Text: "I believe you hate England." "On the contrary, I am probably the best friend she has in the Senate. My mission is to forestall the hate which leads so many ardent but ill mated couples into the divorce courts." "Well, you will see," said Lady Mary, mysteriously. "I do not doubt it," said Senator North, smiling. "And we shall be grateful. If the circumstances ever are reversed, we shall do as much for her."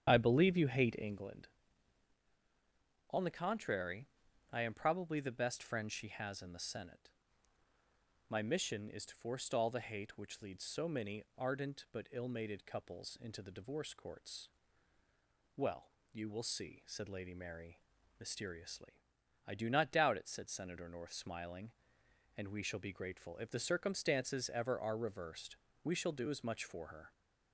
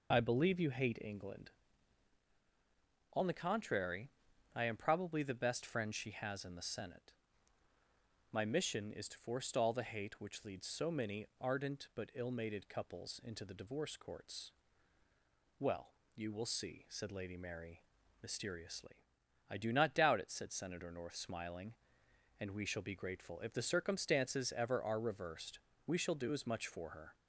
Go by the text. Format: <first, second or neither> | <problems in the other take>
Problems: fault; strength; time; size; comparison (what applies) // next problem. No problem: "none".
second | starts louder than the rest; strong; until 1.3 s; 9 dB